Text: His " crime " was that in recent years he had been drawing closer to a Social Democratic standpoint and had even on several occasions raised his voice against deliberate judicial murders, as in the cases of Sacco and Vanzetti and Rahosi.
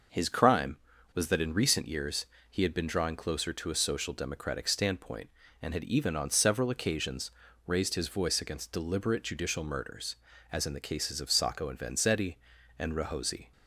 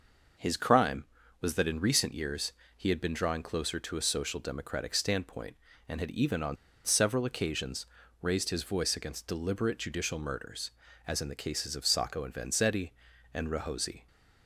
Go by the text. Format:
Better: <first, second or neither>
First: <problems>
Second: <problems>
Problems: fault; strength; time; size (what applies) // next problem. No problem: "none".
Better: first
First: pauses between "years" and "he"; slight; at 2.2 s; 0.24 s long // pauses between "occasions" and "raised"; slight; at 7.2 s; 0.36 s long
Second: pauses between "years" and "he"; slight; at 2.5 s; 0.24 s long // pauses between "on" and "several"; slight; at 6.5 s; 0.28 s long // pauses between "occasions" and "raised"; slight; at 7.8 s; 0.36 s long